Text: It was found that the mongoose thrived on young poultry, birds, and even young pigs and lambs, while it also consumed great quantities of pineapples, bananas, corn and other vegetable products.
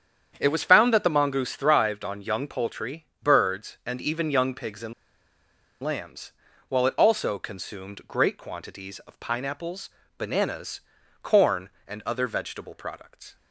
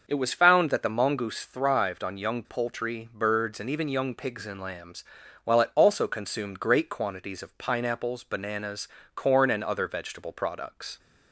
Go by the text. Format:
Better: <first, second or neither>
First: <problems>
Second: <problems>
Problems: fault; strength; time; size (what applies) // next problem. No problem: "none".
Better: second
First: starts louder than the rest; strong; until 1.4 s; 8.5 dB // pauses between "and" and "lambs"; noticeable; at 4.9 s; 0.90 s long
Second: starts louder than the rest; noticeable; until 1.0 s; 6 dB